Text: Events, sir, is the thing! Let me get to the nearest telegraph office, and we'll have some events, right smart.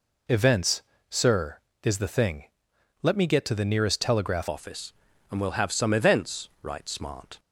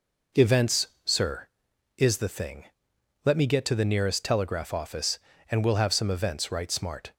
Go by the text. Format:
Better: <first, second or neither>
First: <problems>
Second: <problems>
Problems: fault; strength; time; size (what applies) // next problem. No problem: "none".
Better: second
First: changes voice at "office"; from 4.4 s on; 2.9 s long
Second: none